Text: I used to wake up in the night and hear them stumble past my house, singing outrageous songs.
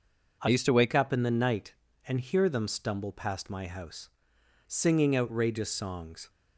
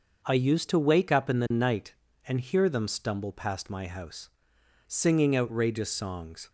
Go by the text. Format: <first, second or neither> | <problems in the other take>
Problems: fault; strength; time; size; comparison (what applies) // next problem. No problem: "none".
second | changes voice from "used" to "wake"; from 0.4 to 0.9 s; 0.5 s long